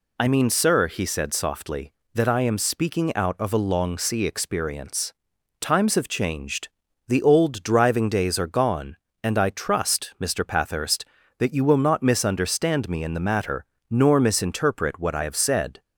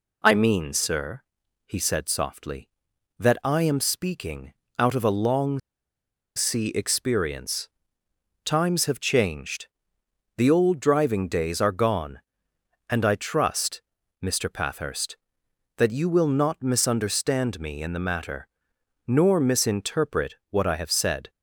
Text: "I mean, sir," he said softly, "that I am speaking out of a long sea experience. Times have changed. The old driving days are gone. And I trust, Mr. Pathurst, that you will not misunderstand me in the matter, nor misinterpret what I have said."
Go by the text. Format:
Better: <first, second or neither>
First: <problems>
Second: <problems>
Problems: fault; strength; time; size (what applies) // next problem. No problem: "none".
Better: first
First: none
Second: pauses between "speaking" and "out"; slight; at 4.5 s; 0.24 s long // pauses between "long" and "sea"; noticeable; at 5.5 s; 0.78 s long